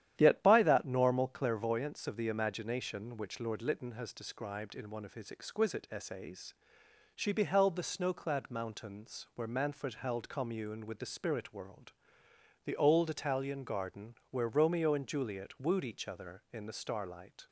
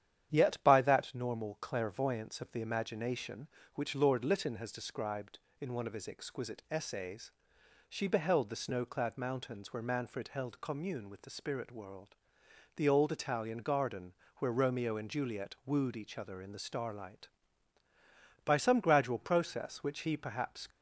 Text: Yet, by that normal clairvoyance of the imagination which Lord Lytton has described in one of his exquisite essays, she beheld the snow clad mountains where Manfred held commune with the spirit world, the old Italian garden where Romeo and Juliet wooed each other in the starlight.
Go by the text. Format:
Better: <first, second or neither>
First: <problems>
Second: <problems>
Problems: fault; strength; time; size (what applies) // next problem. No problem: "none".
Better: first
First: starts louder than the rest; strong; until 1.1 s; 11 dB // pauses between "garden" and "where"; slight; at 14.1 s; 0.16 s long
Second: starts louder than the rest; strong; until 1.3 s; 10 dB // pauses between "garden" and "where"; slight; at 14.1 s; 0.24 s long // goes on to say "By some gradual process which he perhaps"; strong; from 18.4 s on; 2.2 s long